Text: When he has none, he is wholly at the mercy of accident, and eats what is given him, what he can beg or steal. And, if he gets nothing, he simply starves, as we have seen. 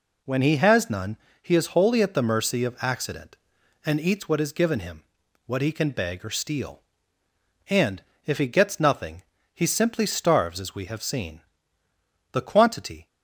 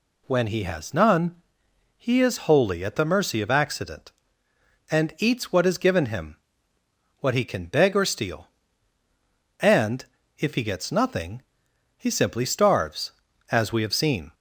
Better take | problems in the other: second | goes on to say "The quantity"; noticeable; from 12.3 s on; 0.76 s long

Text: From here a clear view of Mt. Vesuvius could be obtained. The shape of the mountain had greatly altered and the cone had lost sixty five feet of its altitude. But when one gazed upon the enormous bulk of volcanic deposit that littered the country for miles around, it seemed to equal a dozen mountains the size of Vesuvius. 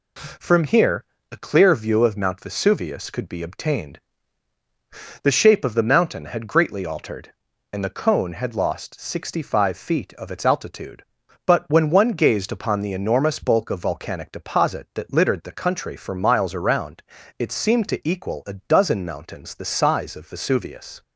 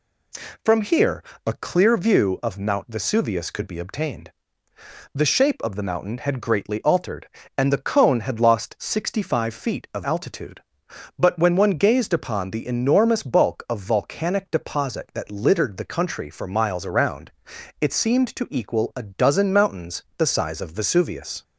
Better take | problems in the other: first | pauses between "here" and "a"; slight; at 1.2 s; 0.22 s long; slight in the first // skips "its"; at 10.0 s

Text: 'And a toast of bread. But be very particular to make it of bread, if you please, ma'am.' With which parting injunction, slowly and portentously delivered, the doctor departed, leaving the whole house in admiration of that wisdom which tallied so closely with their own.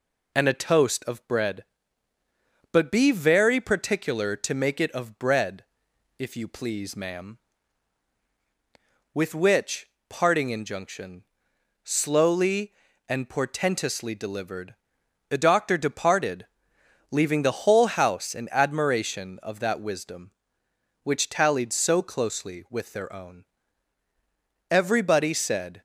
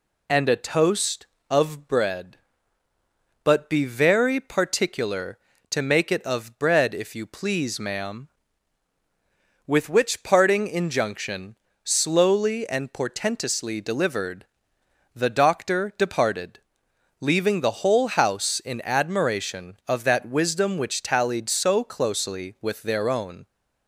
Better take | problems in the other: second | pauses between "which" and "parting"; slight; at 9.8 s; 0.18 s long // goes on to say "Everybody said"; noticeable; from 24.6 s on; 1.1 s long

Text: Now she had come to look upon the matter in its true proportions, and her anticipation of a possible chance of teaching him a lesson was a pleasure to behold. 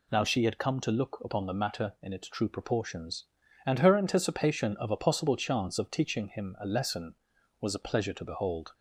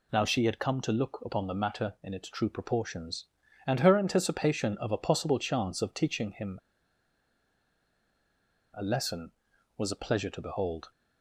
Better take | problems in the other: first | pauses between "him" and "a"; strong; at 6.5 s; 2.1 s long

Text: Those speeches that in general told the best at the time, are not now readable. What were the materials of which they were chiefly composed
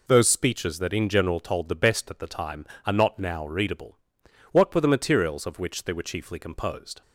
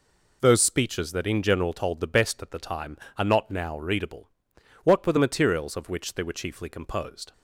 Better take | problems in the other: neither | none

